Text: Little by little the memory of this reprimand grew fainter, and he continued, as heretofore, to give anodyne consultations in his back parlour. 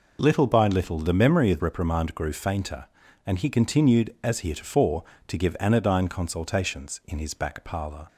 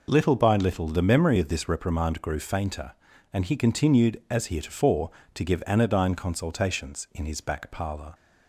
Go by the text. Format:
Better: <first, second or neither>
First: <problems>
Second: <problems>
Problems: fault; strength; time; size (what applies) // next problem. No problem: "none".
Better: second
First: skips "this"; at 1.6 s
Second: none